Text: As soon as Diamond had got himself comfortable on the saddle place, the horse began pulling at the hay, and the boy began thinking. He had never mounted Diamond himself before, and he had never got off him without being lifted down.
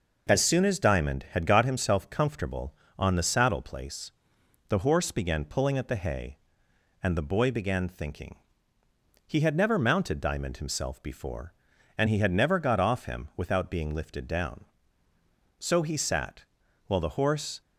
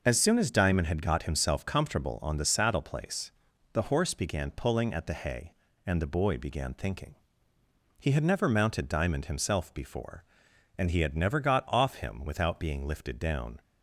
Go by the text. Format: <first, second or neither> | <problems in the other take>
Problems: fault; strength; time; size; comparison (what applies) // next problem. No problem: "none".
second | goes on to say "So he sat while the horse"; strong; from 15.6 s on; 2.0 s long